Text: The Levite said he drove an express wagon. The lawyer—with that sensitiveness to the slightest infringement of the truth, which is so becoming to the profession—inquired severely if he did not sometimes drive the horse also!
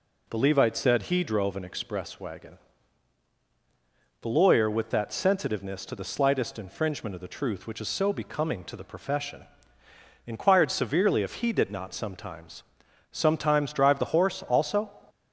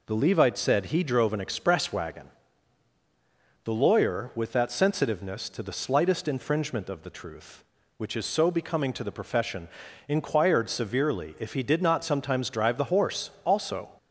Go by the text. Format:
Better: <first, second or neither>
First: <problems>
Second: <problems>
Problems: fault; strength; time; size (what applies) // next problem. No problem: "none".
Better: second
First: says "sometimes" twice; at 13.0 s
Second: none